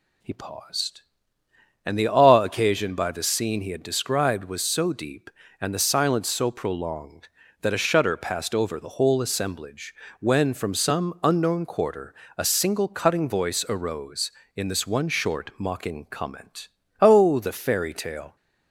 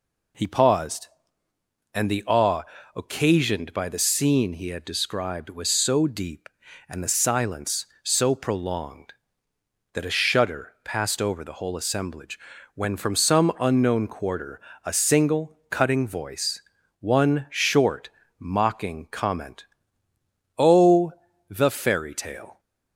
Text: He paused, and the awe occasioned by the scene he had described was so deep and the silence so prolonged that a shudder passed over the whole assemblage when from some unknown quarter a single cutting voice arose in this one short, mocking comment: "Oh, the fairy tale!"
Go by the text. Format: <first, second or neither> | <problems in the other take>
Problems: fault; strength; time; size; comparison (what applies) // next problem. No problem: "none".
first | pauses between "awe" and "occasioned"; slight; at 2.6 s; 0.30 s long // pauses between "assemblage" and "when"; slight; at 12.3 s; 0.36 s long; slight in the first // pauses between "quarter" and "a"; slight; at 14.5 s; 0.24 s long; slight in the first // skips "arose in this"; at 16.7 s